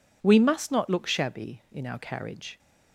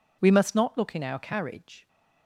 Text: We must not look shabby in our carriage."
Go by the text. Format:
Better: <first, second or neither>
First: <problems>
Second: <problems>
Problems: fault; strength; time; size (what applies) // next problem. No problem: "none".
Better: first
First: none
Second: skips "shabby"; at 0.9 s